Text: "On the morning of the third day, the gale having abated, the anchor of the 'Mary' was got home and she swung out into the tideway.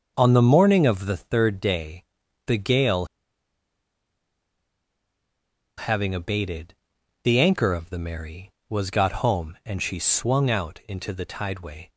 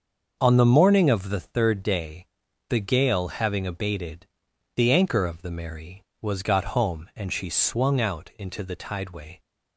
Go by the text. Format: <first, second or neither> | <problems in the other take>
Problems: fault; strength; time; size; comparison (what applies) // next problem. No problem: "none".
second | starts louder than the rest; until 1.1 s; 6.5 dB; also in the second // pauses between "gale" and "having"; strong; at 3.0 s; 2.7 s long